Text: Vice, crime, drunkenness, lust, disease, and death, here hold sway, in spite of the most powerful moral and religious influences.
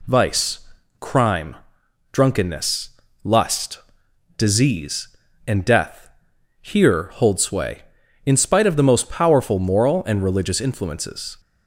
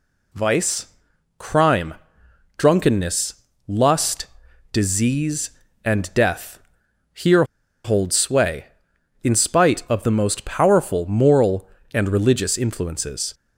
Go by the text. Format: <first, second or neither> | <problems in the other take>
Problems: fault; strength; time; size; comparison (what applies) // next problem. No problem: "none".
first | pauses between "here" and "hold"; at 7.4 s; 0.40 s long